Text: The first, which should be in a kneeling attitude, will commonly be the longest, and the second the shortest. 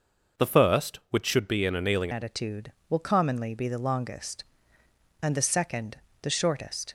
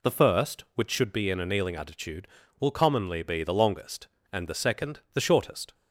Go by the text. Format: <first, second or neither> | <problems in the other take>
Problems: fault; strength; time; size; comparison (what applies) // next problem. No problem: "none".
second | changes voice at "attitude"; from 2.1 s on; 4.8 s long // pauses between "second" and "the"; slight; at 5.9 s; 0.24 s long